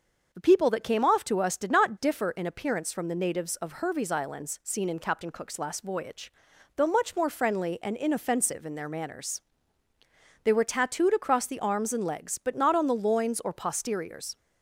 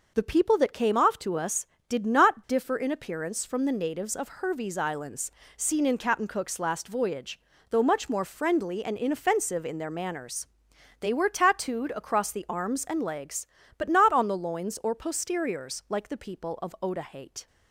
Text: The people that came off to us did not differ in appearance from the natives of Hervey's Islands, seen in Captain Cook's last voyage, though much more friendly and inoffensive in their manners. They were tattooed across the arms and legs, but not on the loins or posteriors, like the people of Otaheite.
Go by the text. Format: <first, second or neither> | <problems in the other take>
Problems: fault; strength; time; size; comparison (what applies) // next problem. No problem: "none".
second | starts louder than the rest; until 1.3 s; 6.5 dB // stops before "like the people of Otaheite"; at 14.3 s